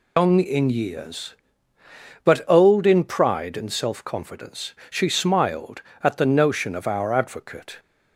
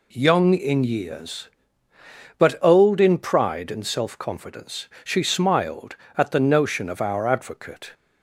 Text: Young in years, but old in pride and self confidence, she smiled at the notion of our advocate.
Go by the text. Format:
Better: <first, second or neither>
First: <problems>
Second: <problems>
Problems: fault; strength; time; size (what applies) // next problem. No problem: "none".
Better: second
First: loses the start of "Young"; at 0.1 s; 180 ms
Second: none